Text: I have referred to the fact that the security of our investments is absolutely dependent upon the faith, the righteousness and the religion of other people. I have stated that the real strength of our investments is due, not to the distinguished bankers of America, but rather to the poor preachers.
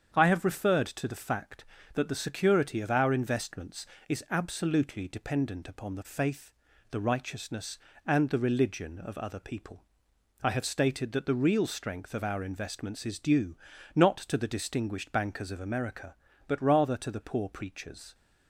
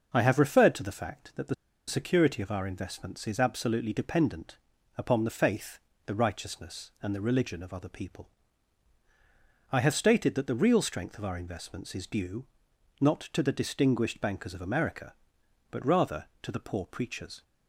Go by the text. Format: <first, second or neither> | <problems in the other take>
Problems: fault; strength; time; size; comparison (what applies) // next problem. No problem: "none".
first | starts louder than the rest; until 1.1 s; 6 dB; strong in the first // pauses between "the" and "security"; slight; at 1.5 s; 0.33 s long // pauses between "dependent" and "upon"; at 4.5 s; 0.40 s long